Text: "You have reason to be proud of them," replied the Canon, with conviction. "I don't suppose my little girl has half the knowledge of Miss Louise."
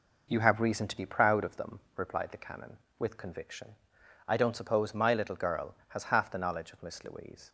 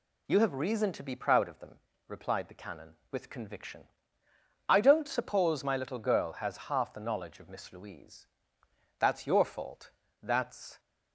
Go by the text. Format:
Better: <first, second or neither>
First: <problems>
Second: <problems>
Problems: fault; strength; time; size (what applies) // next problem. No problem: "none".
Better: first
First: none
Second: goes on to say "That's your fault that's"; strong; from 8.9 s on; 1.8 s long